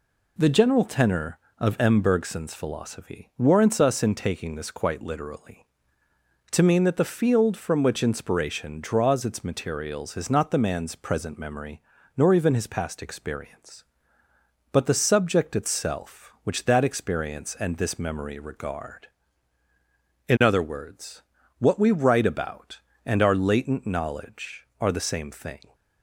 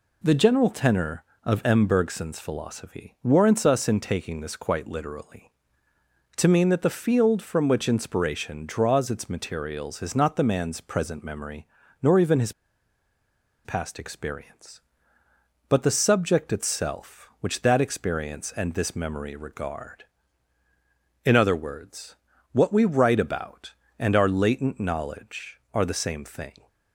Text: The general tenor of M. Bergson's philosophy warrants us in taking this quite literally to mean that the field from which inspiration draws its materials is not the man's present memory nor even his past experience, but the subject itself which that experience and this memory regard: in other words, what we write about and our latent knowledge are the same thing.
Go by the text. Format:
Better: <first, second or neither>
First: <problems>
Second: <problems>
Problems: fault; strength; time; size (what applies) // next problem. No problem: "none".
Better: first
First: pauses between "memory" and "nor"; slight; at 11.8 s; 0.34 s long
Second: pauses between "memory" and "nor"; slight; at 11.6 s; 0.34 s long // pauses between "his" and "past"; at 12.5 s; 1.1 s long